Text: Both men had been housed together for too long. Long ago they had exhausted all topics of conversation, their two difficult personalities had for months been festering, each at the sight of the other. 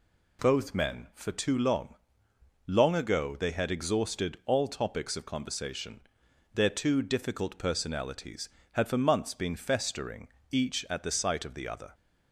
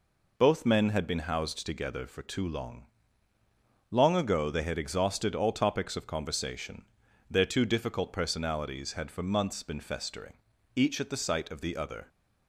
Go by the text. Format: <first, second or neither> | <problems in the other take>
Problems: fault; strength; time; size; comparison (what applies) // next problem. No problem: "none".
second | skips "had been housed together"; at 1.1 s